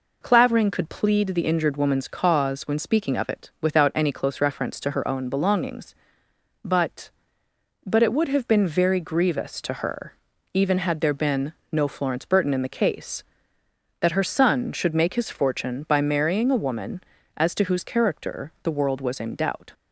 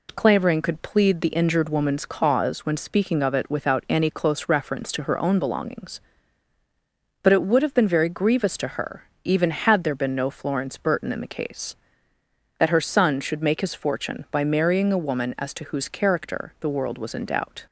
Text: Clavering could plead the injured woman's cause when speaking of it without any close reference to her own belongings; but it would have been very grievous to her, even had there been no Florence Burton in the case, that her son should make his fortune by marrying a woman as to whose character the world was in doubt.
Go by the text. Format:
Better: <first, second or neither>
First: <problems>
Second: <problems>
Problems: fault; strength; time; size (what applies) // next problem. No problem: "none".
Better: second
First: says "but" twice; at 7.8 s // pauses between "been" and "no"; slight; at 11.5 s; 0.20 s long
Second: none